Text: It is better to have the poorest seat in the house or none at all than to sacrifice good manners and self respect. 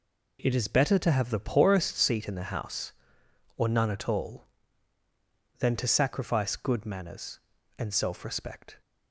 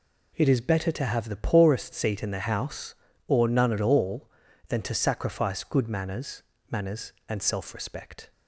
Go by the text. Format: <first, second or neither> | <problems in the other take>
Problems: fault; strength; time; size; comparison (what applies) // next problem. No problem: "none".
first | says "manners" twice; at 6.7 s